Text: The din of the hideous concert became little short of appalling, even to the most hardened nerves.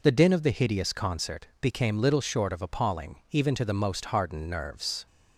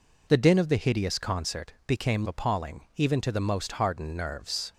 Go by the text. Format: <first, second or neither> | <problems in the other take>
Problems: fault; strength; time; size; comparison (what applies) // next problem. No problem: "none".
first | skips "little short of"; at 2.2 s